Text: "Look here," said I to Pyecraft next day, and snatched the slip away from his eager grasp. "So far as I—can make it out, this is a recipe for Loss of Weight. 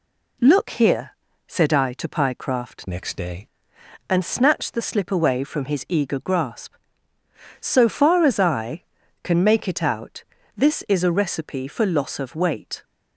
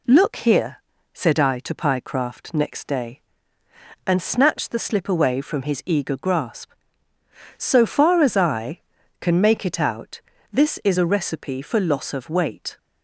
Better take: second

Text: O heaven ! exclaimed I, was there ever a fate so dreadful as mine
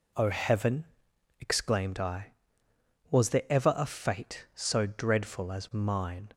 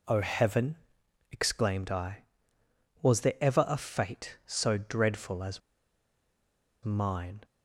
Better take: first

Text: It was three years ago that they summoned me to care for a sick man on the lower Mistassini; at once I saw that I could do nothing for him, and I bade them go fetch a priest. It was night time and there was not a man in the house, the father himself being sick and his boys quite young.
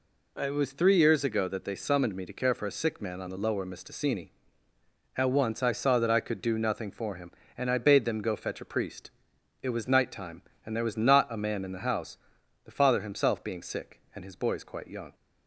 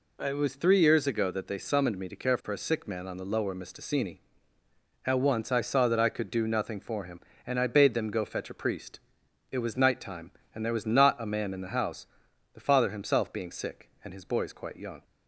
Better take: neither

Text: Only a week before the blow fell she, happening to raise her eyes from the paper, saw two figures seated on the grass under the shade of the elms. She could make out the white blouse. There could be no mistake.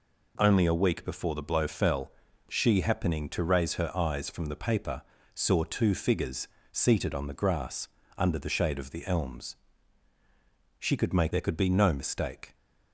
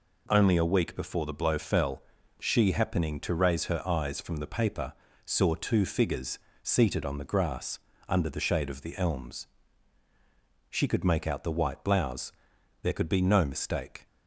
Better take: second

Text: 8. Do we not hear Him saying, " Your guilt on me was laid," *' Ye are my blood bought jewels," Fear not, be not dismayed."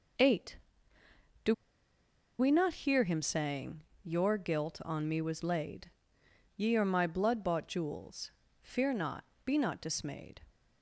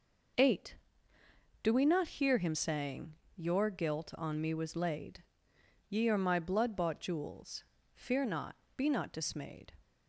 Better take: second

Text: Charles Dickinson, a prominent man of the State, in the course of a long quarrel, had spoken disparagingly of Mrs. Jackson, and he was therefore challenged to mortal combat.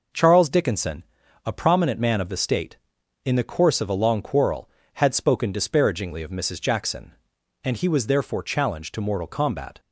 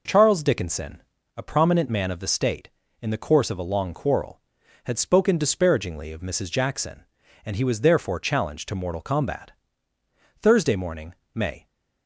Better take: first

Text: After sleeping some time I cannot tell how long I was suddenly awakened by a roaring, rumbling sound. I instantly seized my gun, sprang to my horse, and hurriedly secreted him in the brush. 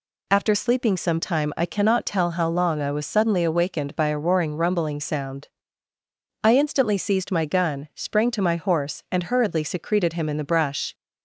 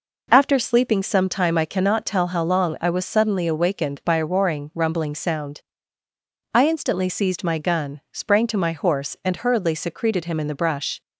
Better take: neither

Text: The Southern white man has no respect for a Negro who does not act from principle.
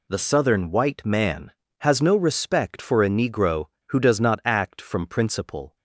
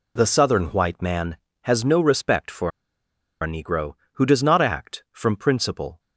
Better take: first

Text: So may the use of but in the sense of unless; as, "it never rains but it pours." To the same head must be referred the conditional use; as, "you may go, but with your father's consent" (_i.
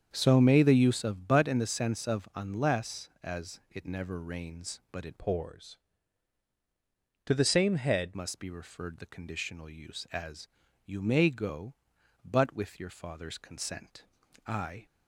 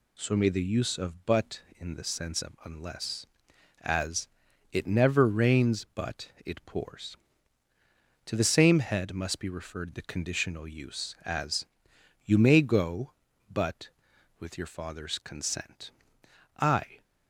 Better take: second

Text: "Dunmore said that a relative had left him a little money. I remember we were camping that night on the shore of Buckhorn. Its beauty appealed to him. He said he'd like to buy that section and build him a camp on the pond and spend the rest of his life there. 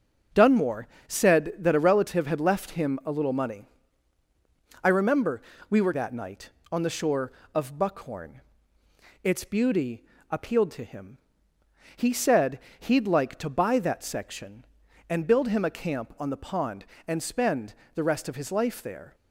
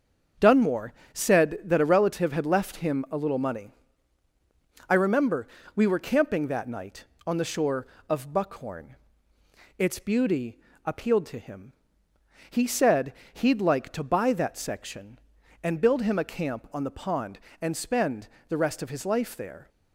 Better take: second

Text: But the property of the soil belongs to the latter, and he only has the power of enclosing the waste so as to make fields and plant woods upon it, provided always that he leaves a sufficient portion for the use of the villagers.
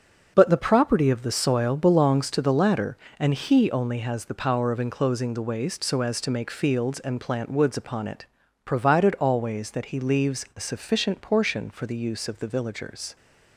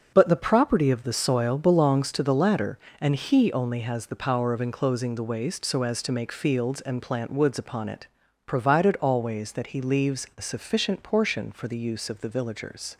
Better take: neither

